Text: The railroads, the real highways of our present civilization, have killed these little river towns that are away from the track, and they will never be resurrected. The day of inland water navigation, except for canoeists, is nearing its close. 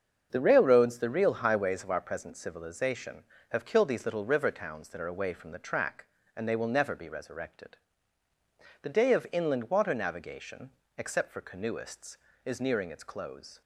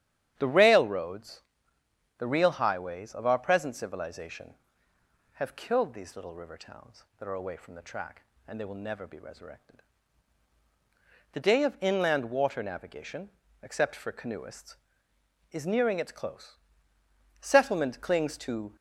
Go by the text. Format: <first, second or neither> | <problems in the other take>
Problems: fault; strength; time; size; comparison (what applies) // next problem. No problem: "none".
first | starts louder than the rest; strong; until 1.3 s; 11.5 dB; also in the first // goes on to say "Settlement clings to"; from 17.3 s on; 1.3 s long